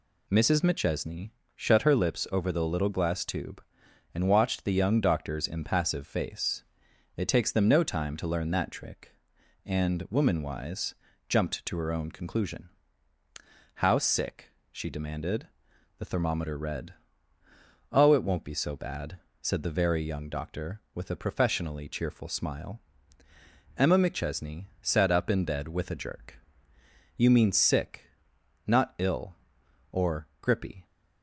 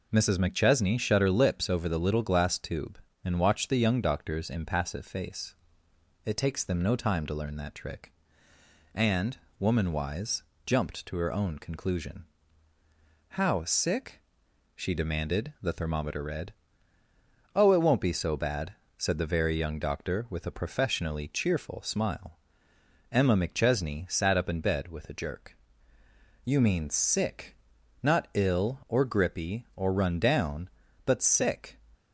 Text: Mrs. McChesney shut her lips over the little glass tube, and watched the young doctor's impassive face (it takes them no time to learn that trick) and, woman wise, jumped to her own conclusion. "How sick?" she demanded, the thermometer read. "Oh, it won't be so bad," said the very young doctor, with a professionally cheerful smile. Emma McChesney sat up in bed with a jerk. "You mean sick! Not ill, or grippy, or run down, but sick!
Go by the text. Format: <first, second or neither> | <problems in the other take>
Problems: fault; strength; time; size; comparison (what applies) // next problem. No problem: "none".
second | pauses between "McChesney" and "shut"; slight; at 1.3 s; 0.24 s long // pauses between "McChesney" and "sat"; slight; at 24.6 s; 0.16 s long // stops before "or run down but sick"; at 30.8 s